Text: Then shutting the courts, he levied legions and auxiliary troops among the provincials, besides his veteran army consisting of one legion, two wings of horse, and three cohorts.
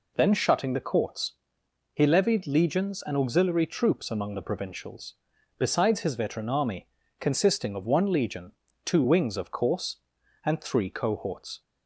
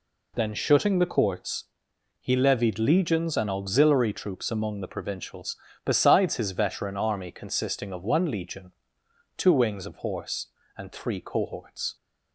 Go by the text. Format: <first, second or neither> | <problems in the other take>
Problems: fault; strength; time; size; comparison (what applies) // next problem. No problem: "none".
second | pauses between "army" and "consisting"; slight; at 6.8 s; 0.34 s long // says "course" for "horse"; at 9.5 s